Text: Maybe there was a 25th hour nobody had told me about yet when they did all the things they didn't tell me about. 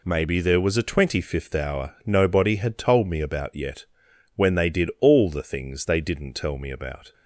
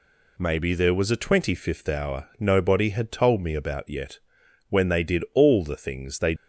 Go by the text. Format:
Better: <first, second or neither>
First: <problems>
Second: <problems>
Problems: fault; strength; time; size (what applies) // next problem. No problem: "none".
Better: first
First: pauses between "yet" and "when"; noticeable; at 3.8 s; 0.50 s long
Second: pauses between "yet" and "when"; noticeable; at 4.1 s; 0.50 s long // stops before "didn't tell me about"; at 6.3 s